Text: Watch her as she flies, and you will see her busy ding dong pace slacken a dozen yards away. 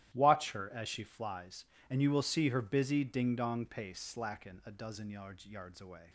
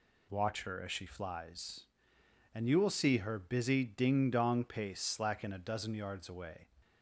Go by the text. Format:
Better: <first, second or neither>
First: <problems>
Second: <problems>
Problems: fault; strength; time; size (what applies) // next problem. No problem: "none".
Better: second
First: starts louder than the rest; strong; until 1.1 s; 13.5 dB // says "yards" twice; at 5.4 s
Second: none